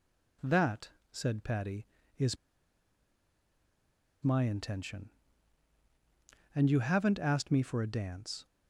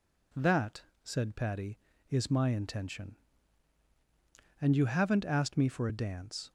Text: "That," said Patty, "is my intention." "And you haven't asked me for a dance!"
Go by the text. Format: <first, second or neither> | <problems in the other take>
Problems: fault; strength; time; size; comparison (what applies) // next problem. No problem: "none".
second | pauses between "is" and "my"; strong; at 2.3 s; 1.8 s long